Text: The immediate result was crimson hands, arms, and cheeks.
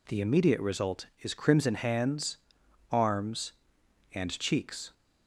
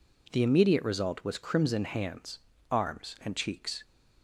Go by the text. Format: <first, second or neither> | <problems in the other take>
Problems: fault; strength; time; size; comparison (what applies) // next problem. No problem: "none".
second | says "is" for "was"; at 1.2 s